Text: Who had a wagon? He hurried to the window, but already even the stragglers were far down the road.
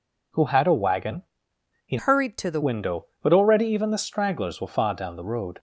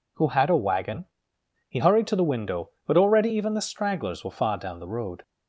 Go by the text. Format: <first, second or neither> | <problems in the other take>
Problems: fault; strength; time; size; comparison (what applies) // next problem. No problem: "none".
second | changes voice from "hurried" to "the"; from 1.9 to 2.6 s; 0.7 s long